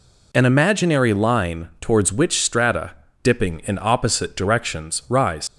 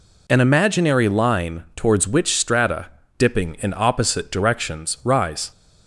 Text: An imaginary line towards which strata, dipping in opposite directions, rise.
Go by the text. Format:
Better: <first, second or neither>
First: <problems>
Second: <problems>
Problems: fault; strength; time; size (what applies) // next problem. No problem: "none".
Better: second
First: leaves "rise" unfinished; at 5.4 s; 80 ms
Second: none